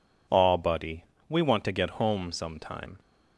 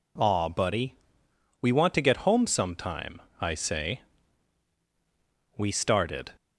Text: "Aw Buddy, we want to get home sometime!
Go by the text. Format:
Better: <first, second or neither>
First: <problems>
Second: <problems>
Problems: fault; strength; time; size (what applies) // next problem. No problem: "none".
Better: first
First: none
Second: goes on to say "I say we started"; strong; from 3.3 s on; 2.9 s long